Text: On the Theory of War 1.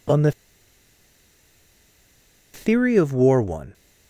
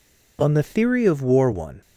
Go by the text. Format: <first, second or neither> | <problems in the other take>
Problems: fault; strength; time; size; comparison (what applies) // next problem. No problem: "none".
second | pauses between "the" and "Theory"; strong; at 0.3 s; 2.2 s long